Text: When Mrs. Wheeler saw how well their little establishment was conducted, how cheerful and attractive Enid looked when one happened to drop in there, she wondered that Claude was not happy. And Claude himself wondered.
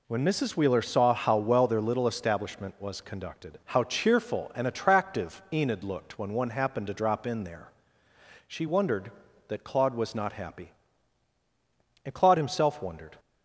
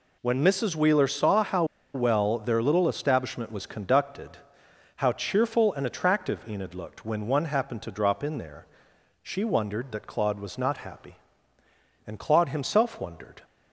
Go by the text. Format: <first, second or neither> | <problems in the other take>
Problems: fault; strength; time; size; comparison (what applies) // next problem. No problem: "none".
first | pauses between "how" and "well"; slight; at 1.6 s; 0.30 s long